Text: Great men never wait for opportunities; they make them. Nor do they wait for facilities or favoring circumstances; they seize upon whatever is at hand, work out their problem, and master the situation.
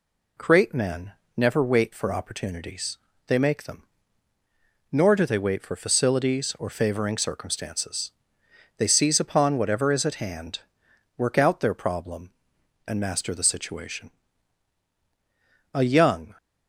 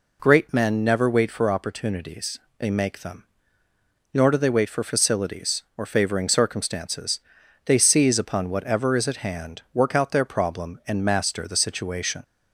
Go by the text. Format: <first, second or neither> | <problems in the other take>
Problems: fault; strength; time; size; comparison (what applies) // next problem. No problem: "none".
second | pauses between "men" and "never"; slight; at 1.1 s; 0.24 s long // goes on to say "A young"; noticeable; from 15.7 s on; 0.62 s long